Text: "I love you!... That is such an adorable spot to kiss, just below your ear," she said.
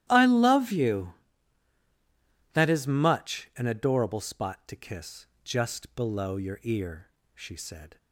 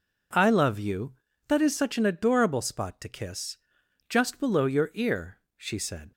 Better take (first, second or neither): second